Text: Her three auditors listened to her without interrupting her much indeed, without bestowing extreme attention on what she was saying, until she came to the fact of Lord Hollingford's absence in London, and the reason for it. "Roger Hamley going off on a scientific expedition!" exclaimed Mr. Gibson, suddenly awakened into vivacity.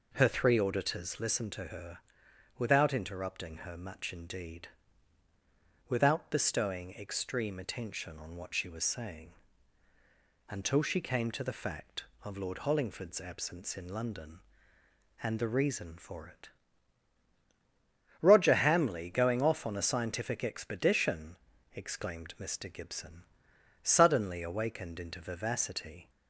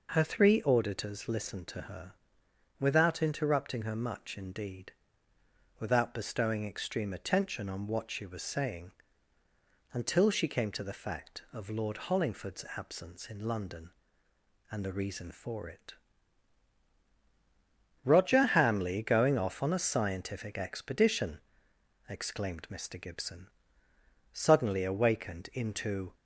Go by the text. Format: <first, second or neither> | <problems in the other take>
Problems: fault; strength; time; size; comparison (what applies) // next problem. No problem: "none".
first | pauses between "her" and "without"; noticeable; at 2.1 s; 0.66 s long; noticeable in the first // stops before "vivacity"; at 26.1 s